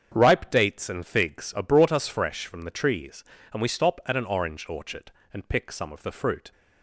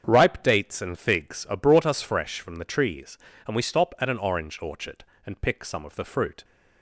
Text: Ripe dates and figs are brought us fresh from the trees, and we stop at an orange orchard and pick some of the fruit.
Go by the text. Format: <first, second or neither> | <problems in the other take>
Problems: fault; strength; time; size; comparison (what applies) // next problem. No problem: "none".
neither | starts louder than the rest; strong; the same in both